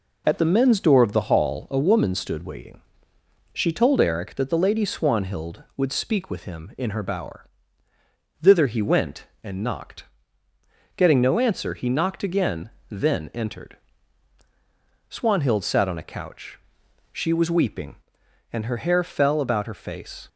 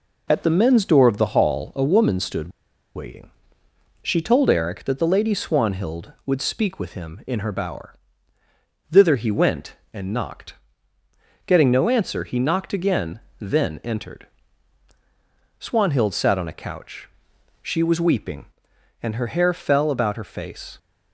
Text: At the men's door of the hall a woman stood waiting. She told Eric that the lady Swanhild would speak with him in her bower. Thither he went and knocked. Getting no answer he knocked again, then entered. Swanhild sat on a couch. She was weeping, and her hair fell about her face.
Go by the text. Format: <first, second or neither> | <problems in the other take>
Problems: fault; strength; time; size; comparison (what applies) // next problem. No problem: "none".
first | pauses between "stood" and "waiting"; at 2.4 s; 0.45 s long